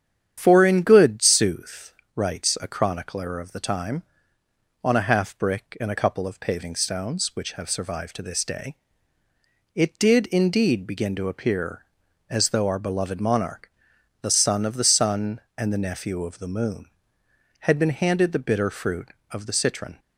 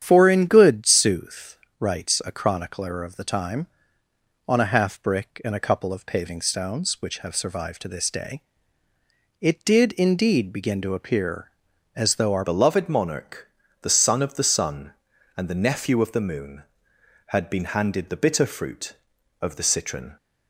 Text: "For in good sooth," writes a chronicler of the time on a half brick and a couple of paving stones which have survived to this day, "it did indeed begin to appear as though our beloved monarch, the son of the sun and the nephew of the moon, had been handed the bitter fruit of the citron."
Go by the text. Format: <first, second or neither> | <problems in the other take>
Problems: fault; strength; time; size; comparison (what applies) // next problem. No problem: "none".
first | starts louder than the rest; strong; until 1.0 s; 9.5 dB; strong in the first // changes voice at "beloved"; from 12.4 s on; 7.7 s long